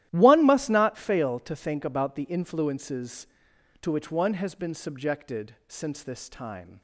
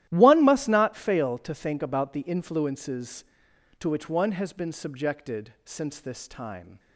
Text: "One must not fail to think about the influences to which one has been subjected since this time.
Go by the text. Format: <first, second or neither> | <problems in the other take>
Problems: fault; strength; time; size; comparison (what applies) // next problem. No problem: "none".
neither | starts louder than the rest; strong; the same in both